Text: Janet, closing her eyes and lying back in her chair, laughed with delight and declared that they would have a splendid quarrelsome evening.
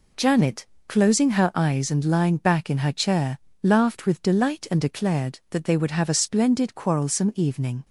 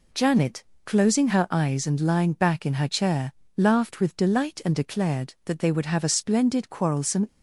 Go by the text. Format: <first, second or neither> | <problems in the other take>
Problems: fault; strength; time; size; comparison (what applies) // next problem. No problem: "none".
first | stops before "evening"; at 7.2 s